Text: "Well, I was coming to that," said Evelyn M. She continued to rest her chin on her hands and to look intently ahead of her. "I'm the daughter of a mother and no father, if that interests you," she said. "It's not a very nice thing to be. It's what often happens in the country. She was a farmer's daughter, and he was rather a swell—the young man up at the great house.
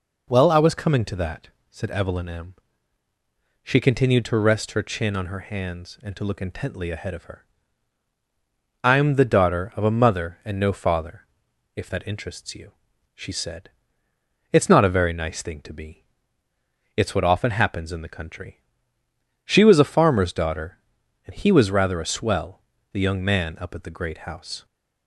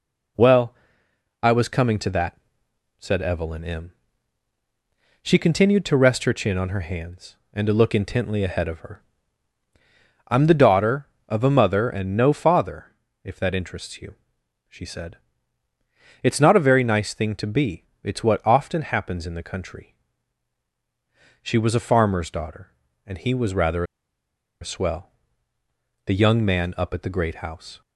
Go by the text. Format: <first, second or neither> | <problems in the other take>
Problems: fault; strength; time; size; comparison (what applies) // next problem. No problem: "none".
first | pauses between "rather" and "a"; noticeable; at 23.8 s; 0.77 s long